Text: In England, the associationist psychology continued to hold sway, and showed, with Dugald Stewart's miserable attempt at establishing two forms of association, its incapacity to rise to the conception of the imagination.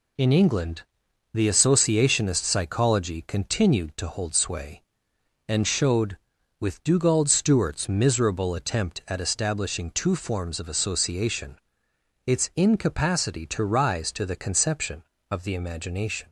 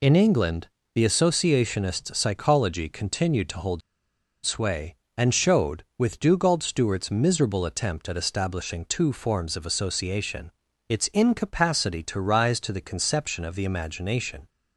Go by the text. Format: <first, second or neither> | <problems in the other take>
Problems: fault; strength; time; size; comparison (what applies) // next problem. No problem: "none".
first | pauses between "hold" and "sway"; noticeable; at 3.8 s; 0.63 s long